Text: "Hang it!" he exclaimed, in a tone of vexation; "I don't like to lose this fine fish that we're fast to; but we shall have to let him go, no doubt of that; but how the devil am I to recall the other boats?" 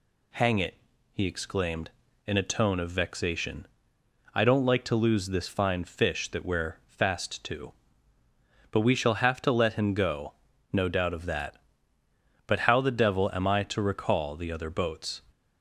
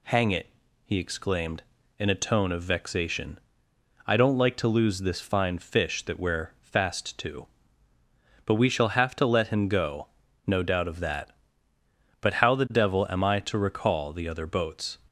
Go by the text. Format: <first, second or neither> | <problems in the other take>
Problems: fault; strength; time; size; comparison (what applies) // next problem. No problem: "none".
neither | none